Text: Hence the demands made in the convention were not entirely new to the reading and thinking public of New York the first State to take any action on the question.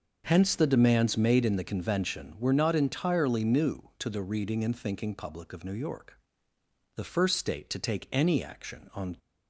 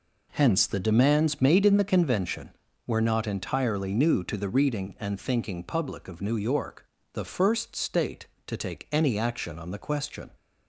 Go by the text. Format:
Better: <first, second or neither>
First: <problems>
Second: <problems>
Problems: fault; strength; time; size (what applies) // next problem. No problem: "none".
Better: second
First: starts louder than the rest; until 1.2 s; 6 dB // pauses between "York" and "the"; noticeable; at 6.1 s; 0.78 s long // stops before "the question"; at 9.1 s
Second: pauses between "York" and "the"; slight; at 6.8 s; 0.28 s long